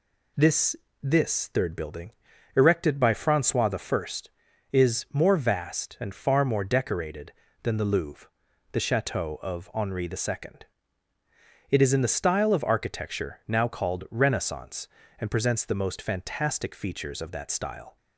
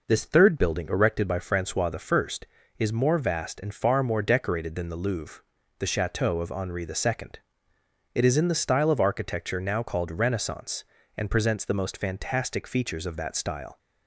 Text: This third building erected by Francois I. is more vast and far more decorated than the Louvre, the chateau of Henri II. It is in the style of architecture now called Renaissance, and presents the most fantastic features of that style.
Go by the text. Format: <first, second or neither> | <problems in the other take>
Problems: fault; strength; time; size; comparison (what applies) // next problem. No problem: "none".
second | says "This" twice; at 1.0 s // pauses between "building" and "erected"; at 2.1 s; 0.44 s long